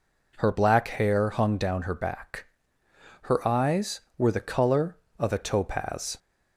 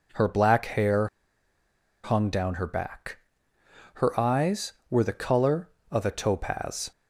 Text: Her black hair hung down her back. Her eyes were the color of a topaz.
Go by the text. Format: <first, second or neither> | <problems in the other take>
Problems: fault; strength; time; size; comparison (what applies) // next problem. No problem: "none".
first | pauses between "hair" and "hung"; noticeable; at 1.0 s; 0.97 s long